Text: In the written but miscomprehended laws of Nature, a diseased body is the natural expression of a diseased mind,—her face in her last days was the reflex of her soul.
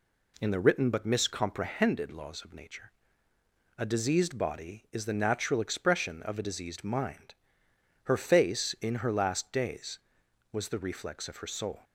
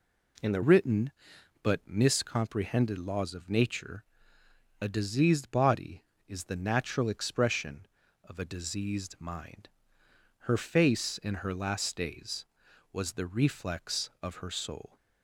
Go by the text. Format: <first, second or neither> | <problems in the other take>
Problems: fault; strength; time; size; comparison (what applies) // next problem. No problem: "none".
first | changes voice at "written"; from 0.6 s on; 14.3 s long